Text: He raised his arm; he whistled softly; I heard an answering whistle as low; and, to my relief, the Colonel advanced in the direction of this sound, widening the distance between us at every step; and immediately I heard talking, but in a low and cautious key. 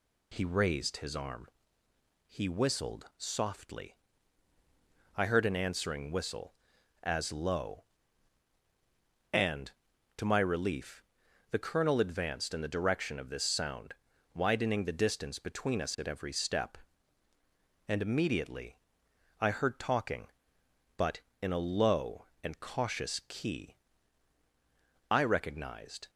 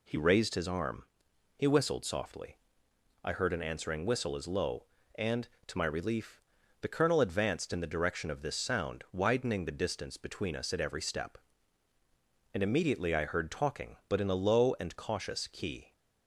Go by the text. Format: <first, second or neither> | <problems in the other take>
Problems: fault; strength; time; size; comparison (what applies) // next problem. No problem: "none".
second | pauses between "immediately" and "I"; noticeable; at 18.7 s; 0.64 s long // goes on to say "I recognized"; noticeable; from 25.0 s on; 1.0 s long